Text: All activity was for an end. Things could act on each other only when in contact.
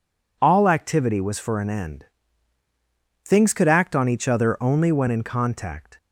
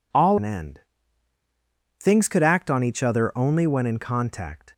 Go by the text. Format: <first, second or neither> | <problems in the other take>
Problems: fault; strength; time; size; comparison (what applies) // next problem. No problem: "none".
first | skips "activity was for"; at 0.3 s